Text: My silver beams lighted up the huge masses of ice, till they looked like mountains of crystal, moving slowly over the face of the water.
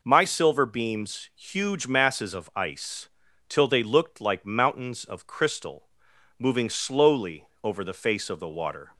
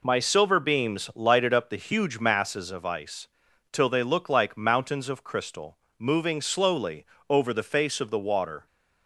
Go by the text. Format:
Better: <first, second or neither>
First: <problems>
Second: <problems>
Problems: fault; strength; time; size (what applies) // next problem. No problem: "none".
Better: second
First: skips "lighted up the"; at 1.3 s // pauses between "slowly" and "over"; slight; at 7.4 s; 0.16 s long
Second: pauses between "slowly" and "over"; slight; at 7.0 s; 0.24 s long